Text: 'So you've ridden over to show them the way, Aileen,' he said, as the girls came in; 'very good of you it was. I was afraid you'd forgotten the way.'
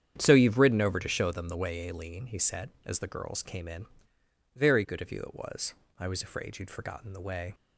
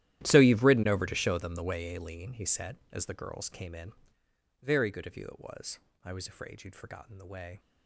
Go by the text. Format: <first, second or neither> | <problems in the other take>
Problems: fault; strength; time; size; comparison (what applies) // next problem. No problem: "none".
first | gets quieter; strong; throughout; 18 dB // starts louder than the rest; strong; until 1.2 s; 13 dB; strong in the first